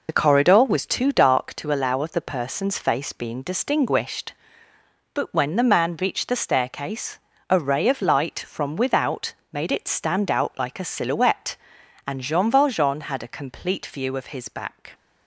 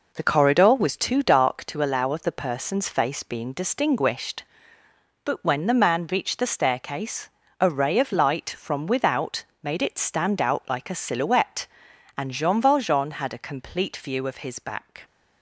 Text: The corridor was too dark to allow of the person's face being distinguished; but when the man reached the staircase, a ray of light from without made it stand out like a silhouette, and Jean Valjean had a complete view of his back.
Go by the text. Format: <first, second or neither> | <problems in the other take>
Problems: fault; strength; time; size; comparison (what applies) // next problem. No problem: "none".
second | loses the start of "The"; at 0.0 s; 50 ms // pauses between "without" and "made"; slight; at 9.3 s; 0.18 s long; slight in the second